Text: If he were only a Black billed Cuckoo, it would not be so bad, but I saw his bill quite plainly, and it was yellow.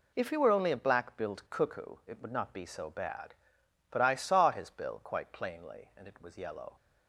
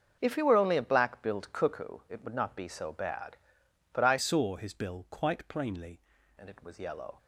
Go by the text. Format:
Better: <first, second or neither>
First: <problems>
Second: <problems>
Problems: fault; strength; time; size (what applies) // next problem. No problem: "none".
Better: first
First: none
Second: starts louder than the rest; until 1.2 s; 6.5 dB // changes voice from "saw" to "plainly"; from 4.1 to 5.9 s; 1.8 s long